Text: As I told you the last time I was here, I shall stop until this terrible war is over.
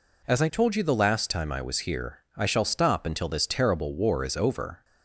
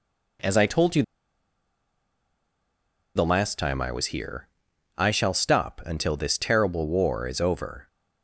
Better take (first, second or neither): first